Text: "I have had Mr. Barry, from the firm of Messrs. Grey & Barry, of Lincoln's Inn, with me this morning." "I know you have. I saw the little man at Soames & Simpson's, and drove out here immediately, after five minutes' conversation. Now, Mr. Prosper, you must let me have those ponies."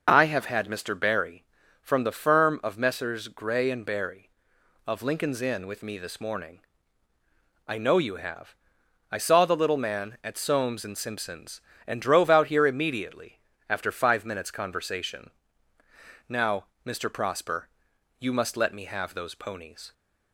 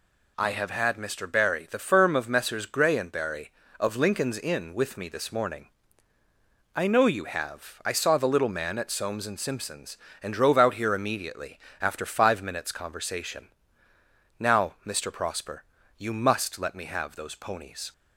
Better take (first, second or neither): first